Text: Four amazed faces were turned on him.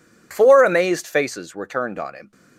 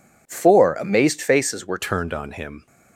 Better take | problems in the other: first | changes voice at "turned"; from 1.7 s on; 0.9 s long

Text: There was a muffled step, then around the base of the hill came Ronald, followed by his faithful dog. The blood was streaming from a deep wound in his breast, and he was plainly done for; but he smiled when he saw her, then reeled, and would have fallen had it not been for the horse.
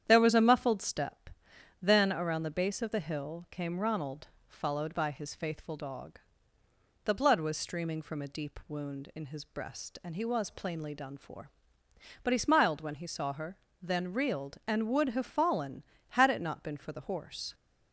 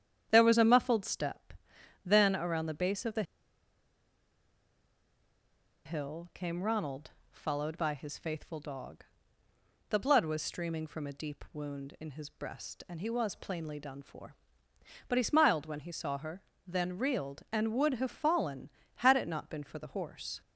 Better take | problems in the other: first | starts louder than the rest; strong; until 1.3 s; 9 dB; strong in the first // pauses between "the" and "hill"; strong; at 3.2 s; 2.6 s long

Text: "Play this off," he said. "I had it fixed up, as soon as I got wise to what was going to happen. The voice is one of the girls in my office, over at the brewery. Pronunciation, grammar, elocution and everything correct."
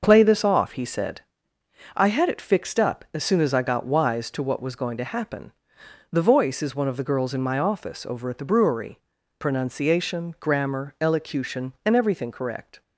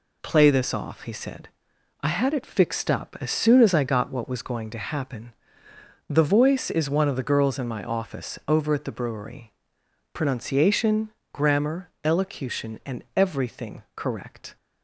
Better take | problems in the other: first | skips "wise to"; at 4.1 s

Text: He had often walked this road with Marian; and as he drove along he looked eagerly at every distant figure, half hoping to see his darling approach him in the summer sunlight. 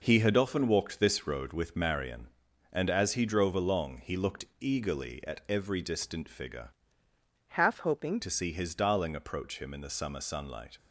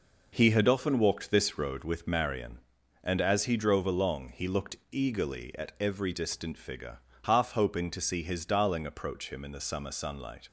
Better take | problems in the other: second | changes voice from "half" to "hoping"; from 7.4 to 8.2 s; 0.8 s long

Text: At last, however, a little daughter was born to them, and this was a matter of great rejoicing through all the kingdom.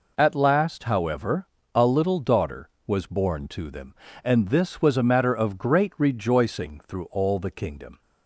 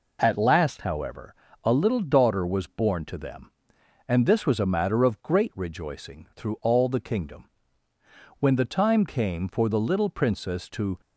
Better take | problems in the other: first | goes on to say "When the time came for the little Princess to"; strong; from 8.3 s on; 2.6 s long

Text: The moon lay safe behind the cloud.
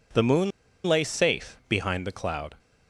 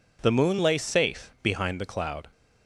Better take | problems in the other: second | pauses between "moon" and "lay"; at 0.5 s; 0.36 s long

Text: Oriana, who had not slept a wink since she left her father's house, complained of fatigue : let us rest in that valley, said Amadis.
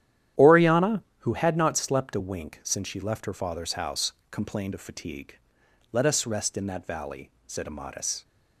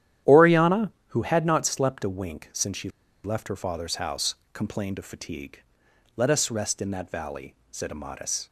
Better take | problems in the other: first | starts louder than the rest; strong; until 1.4 s; 11 dB; strong in the first // pauses between "she" and "left"; slight; at 2.8 s; 0.35 s long

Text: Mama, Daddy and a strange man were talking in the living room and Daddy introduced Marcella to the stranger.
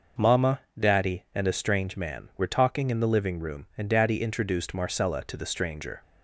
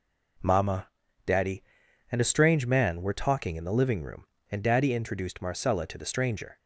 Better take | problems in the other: neither | none

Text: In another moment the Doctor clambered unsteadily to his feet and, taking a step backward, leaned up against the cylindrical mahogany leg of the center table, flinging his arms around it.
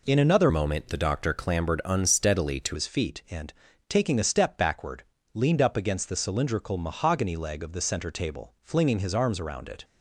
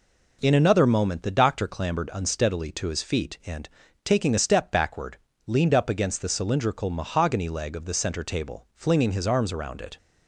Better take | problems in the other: second | changes voice from "moment" to "to"; from 0.4 to 2.7 s; 2.3 s long

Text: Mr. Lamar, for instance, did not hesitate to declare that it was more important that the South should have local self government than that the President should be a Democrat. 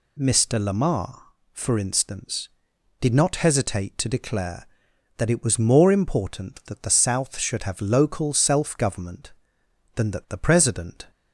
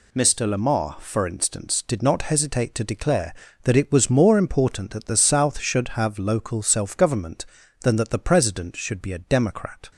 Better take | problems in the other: second | stops before "should be a Democrat"; at 11.1 s

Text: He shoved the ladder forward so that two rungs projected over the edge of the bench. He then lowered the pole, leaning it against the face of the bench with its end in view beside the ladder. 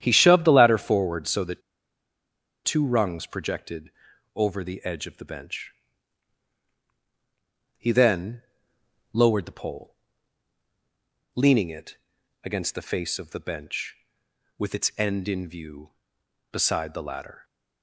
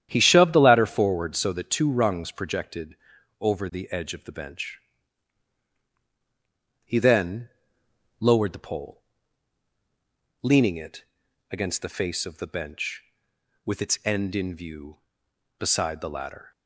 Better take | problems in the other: second | starts louder than the rest; strong; until 1.0 s; 10 dB; strong in the second // pauses between "that" and "two"; at 1.6 s; 1.0 s long // pauses between "projected" and "over"; at 3.9 s; 0.44 s long; also in the second // pauses between "then" and "lowered"; noticeable; at 8.4 s; 0.72 s long; noticeable in the second // pauses between "it" and "against"; noticeable; at 11.9 s; 0.46 s long; noticeable in the second

